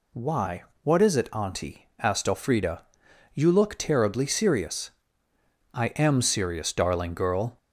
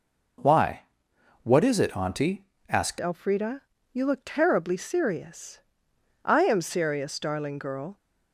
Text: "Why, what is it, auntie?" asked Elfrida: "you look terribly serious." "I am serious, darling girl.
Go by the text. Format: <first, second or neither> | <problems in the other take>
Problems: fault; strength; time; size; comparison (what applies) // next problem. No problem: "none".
first | changes voice at "Elfrida"; from 2.9 s on; 5.0 s long